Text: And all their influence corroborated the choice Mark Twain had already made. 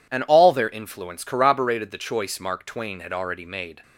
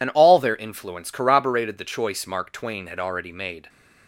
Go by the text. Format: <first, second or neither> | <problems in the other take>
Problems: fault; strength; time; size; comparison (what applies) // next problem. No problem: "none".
first | loses the start of "And"; at 0.0 s; 45 ms